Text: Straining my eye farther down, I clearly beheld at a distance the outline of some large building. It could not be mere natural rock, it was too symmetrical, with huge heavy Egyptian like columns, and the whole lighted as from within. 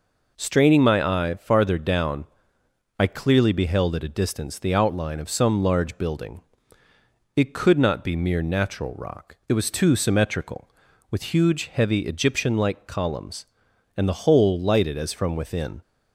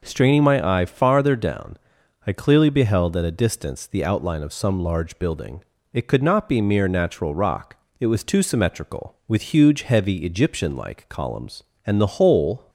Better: first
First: none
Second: stops before "lighted as from within"; at 12.6 s

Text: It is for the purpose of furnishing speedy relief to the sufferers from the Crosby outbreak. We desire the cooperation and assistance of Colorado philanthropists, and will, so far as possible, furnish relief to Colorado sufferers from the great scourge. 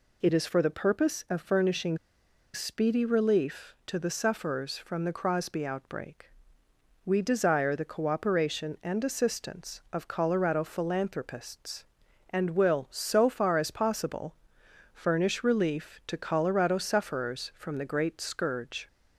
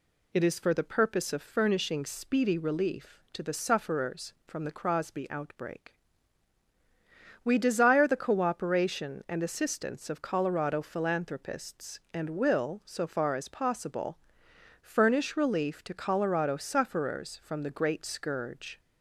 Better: second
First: pauses between "furnishing" and "speedy"; noticeable; at 1.9 s; 0.56 s long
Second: none

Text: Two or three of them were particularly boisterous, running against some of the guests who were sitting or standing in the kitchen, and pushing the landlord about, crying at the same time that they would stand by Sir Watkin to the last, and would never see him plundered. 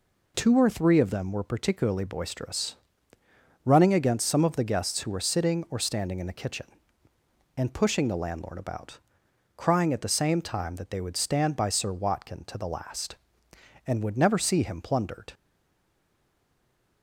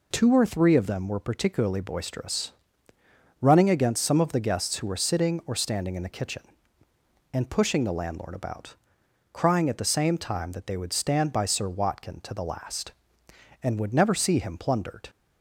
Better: second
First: stays silent after the last word; noticeable; from 15.3 s on; 1.7 s long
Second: none

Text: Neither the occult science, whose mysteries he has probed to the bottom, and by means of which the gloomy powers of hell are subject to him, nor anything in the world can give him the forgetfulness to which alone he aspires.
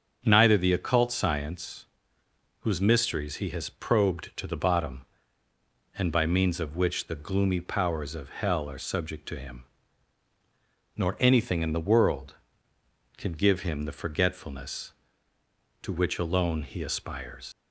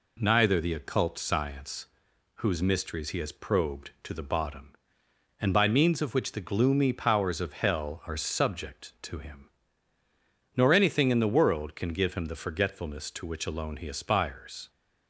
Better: second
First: starts louder than the rest; until 1.2 s; 6.5 dB // leaves "aspires" unfinished; at 17.5 s; 90 ms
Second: none

